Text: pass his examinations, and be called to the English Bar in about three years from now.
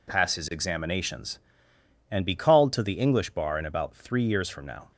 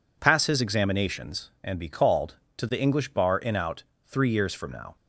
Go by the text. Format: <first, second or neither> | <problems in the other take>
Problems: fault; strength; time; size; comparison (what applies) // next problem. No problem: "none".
first | says "out" for "about"; at 3.5 s